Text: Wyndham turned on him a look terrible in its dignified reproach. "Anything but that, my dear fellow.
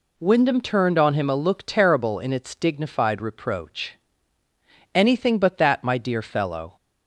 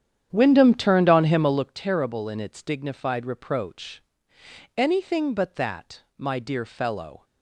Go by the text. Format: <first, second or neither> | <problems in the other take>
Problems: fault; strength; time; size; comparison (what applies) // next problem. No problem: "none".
first | starts louder than the rest; strong; until 1.7 s; 9.5 dB